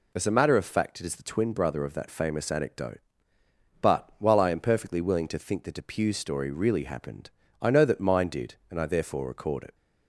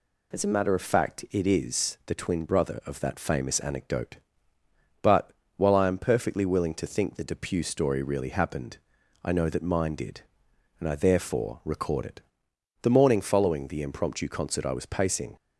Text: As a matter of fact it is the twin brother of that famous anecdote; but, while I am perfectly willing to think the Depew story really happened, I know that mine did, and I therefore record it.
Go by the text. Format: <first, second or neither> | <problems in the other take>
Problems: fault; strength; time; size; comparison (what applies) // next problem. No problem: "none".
first | goes on to say "The morning following the impromptu concert I was pacing"; strong; from 12.8 s on; 2.5 s long